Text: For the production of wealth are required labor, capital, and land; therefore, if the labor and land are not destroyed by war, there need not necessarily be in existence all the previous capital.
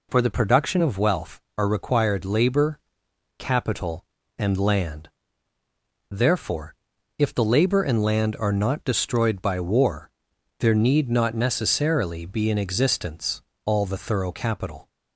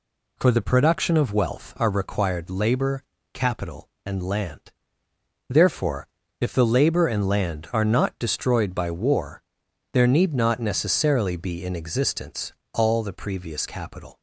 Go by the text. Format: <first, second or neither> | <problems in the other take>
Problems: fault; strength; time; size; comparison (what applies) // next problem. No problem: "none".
second | pauses between "existence" and "all"; slight; at 13.4 s; 0.24 s long; slight in the second // says "thorough" for "previous"; at 13.9 s